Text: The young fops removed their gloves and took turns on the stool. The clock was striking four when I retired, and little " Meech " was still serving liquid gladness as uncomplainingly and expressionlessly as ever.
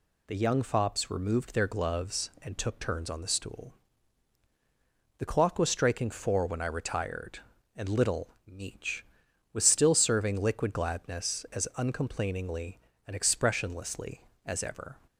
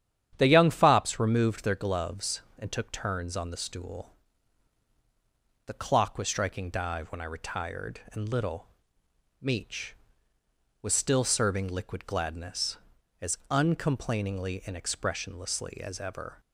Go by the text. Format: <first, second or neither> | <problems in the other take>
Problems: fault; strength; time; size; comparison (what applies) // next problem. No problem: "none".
first | starts louder than the rest; strong; until 1.3 s; 11 dB // says "dive" for "four"; at 6.6 s